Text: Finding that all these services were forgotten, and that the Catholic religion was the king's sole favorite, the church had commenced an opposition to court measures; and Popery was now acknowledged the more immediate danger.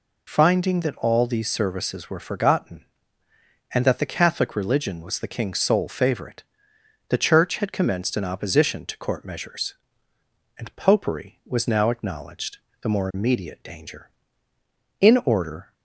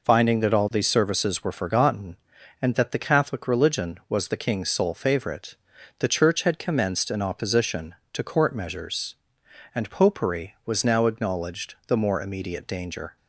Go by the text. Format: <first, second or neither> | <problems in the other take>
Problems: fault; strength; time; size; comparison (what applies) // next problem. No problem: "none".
second | pauses between "acknowledged" and "the"; slight; at 12.5 s; 0.24 s long // goes on to say "In order"; noticeable; from 15.0 s on; 0.72 s long